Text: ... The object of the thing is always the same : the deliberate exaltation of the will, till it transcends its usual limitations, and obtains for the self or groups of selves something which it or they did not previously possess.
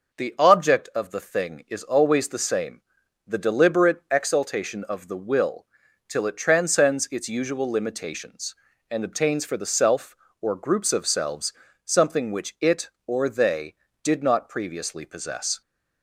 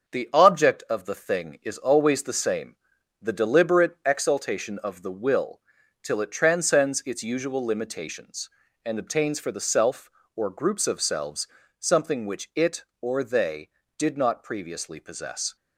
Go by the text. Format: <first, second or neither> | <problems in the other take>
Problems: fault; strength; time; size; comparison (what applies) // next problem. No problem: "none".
first | gets quieter; slight; throughout; 3 dB // pauses between "selves" and "something"; slight; at 11.4 s; 0.32 s long; slight in the first